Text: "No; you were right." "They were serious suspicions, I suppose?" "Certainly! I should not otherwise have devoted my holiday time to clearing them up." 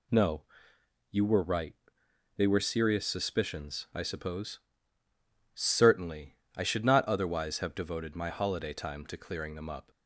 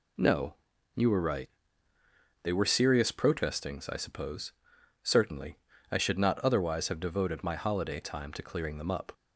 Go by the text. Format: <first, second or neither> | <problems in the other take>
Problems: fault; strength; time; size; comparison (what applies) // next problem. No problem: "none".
first | says "protestings" for "suspicions"; at 3.1 s